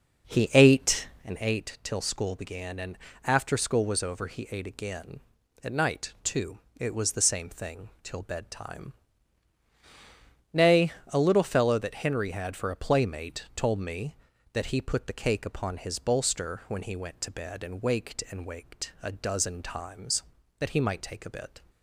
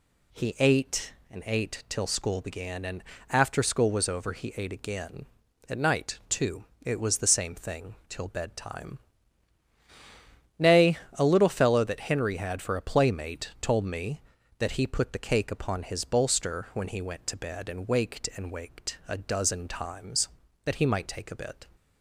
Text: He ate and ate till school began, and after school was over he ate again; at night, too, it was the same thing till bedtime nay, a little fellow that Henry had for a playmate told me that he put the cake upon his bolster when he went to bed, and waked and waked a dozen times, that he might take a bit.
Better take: second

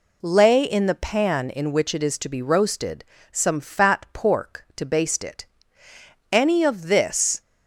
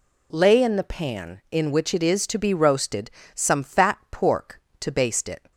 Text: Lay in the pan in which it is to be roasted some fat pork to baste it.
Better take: second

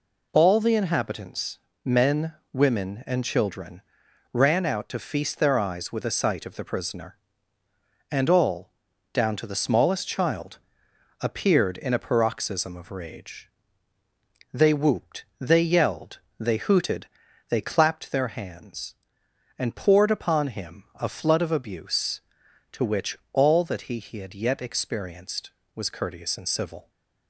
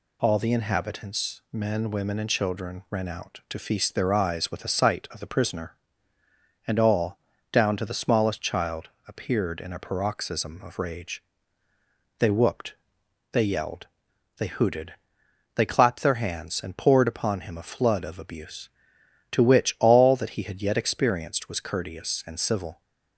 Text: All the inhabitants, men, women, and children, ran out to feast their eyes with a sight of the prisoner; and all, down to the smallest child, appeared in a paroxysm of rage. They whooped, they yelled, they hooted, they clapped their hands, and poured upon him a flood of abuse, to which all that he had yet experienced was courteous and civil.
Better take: second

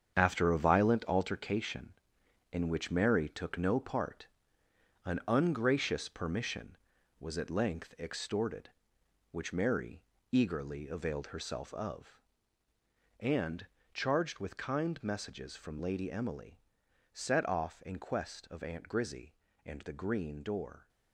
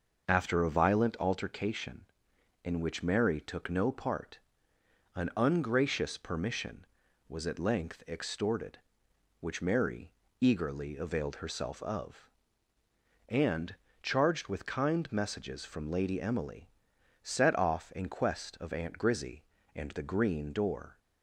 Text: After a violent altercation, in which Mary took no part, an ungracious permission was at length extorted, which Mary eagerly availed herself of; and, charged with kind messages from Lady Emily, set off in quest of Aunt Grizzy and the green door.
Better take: second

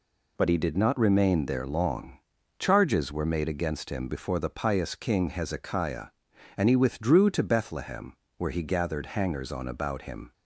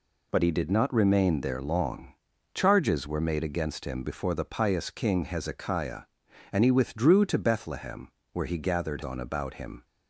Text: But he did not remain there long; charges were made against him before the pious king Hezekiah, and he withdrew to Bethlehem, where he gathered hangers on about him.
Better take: first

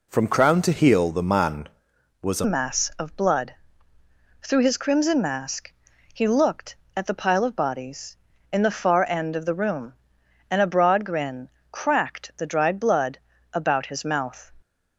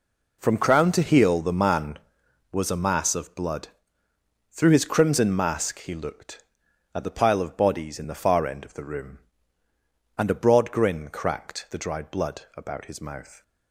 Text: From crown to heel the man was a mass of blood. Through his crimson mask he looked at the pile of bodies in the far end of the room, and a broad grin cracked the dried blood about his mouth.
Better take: second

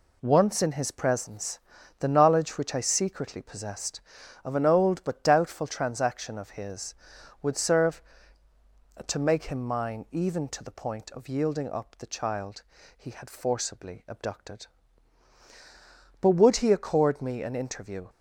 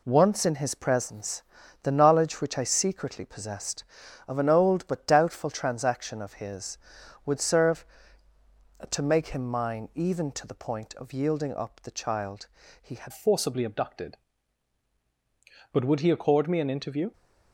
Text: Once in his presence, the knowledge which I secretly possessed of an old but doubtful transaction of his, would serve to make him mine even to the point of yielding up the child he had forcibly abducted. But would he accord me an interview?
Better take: first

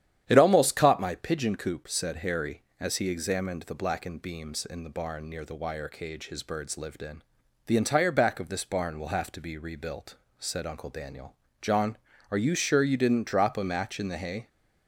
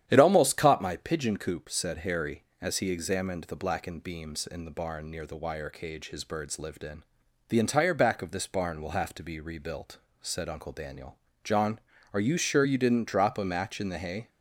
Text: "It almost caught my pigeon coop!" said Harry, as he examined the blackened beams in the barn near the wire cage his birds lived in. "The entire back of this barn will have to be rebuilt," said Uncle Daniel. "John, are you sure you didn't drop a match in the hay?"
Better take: neither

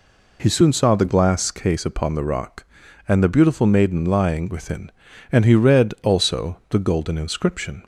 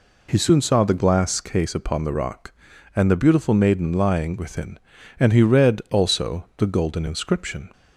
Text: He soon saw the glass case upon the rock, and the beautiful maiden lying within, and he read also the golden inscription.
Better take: neither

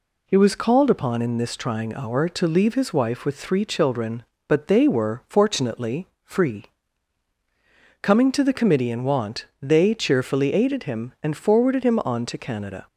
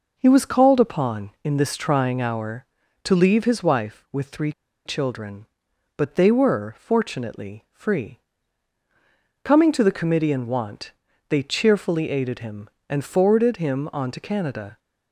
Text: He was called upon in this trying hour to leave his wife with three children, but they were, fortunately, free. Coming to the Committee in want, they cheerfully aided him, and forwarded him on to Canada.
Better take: first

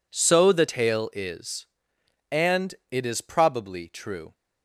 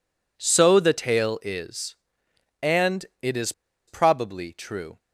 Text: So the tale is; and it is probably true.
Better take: first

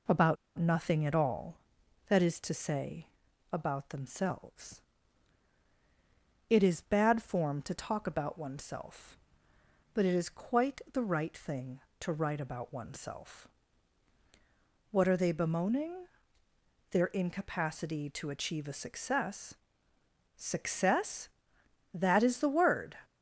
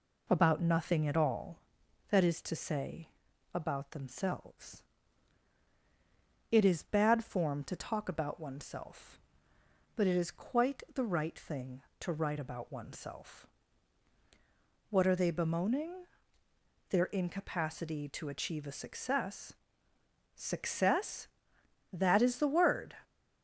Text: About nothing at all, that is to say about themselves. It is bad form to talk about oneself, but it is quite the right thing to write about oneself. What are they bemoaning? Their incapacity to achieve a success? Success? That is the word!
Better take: second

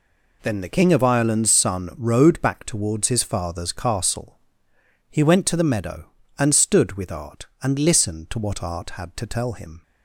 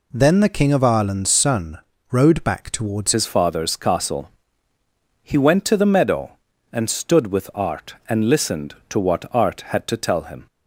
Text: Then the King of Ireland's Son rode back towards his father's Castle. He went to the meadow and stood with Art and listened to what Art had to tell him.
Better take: first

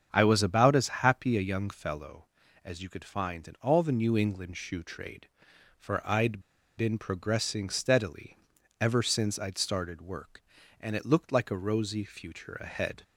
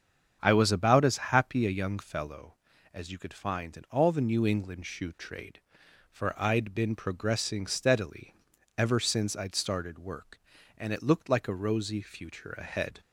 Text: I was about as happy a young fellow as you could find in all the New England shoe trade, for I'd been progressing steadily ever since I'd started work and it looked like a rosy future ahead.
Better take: second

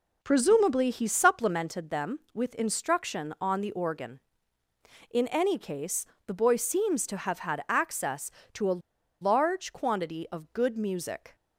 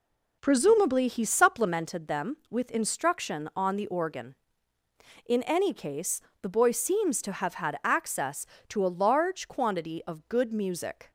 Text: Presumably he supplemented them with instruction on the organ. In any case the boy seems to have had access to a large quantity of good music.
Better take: second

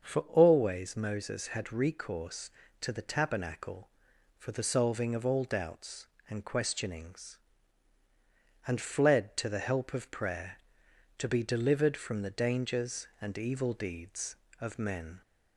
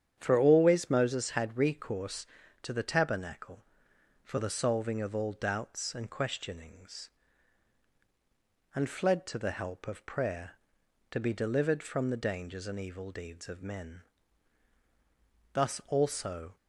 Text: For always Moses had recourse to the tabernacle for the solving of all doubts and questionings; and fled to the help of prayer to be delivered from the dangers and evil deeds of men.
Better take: first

